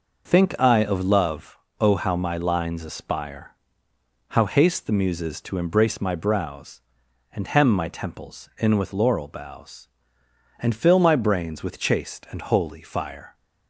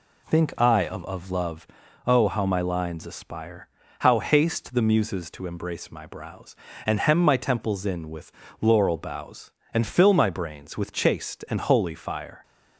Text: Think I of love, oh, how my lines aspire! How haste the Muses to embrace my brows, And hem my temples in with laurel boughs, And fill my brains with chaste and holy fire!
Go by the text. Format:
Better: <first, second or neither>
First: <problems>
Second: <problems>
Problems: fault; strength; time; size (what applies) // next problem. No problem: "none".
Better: first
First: none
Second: says "of" twice; at 1.0 s // pauses between "with" and "laurel"; slight; at 8.3 s; 0.28 s long